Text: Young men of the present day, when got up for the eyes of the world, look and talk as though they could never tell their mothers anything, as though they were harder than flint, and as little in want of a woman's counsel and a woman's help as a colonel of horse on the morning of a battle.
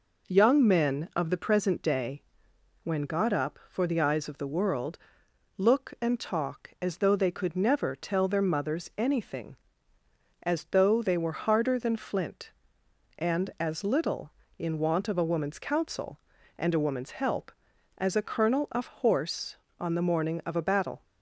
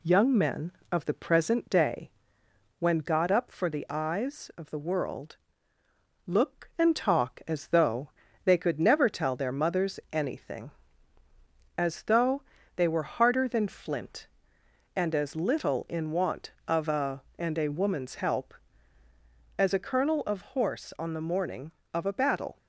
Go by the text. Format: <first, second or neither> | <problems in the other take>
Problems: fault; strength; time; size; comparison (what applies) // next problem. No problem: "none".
first | pauses between "though" and "they"; slight; at 8.1 s; 0.34 s long // pauses between "though" and "they"; slight; at 12.4 s; 0.34 s long // skips "woman's counsel"; at 17.2 s